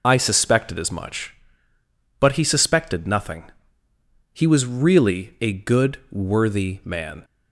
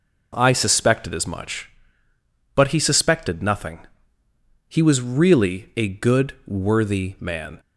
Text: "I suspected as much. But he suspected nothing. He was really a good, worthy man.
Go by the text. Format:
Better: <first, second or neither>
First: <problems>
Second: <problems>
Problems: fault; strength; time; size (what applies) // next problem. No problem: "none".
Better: second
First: loses the start of "I"; at 0.0 s; 75 ms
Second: none